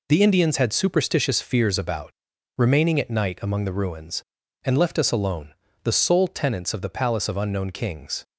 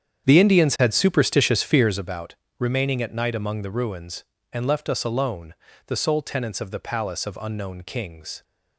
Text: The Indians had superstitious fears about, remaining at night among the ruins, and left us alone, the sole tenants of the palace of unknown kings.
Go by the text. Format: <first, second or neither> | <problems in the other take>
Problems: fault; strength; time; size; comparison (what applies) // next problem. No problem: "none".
first | starts louder than the rest; strong; until 2.1 s; 8.5 dB